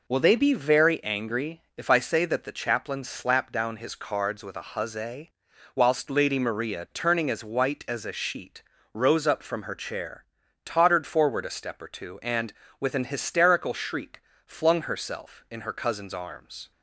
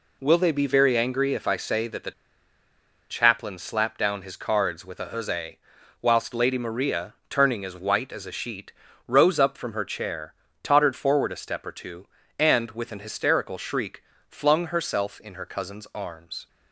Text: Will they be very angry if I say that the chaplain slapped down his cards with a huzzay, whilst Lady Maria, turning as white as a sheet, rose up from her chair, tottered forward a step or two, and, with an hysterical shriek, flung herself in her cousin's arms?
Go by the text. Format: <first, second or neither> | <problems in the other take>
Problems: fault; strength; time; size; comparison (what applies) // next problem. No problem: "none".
first | pauses between "the" and "chaplain"; at 2.1 s; 0.98 s long